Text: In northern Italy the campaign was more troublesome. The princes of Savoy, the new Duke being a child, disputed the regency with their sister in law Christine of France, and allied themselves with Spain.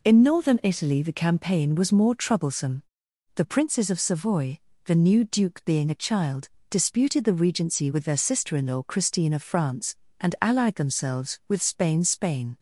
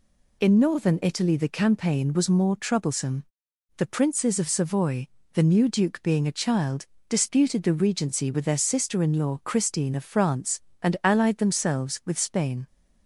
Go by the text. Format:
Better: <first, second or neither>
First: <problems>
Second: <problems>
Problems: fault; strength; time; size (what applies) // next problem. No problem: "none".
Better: second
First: says "Spain" twice; at 12.0 s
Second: none